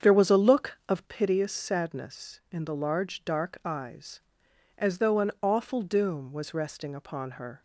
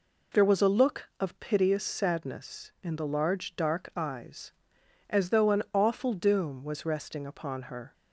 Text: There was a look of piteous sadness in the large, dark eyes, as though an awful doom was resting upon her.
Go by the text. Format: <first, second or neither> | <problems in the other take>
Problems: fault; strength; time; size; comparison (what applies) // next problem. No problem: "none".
second | starts louder than the rest; strong; until 1.1 s; 7.5 dB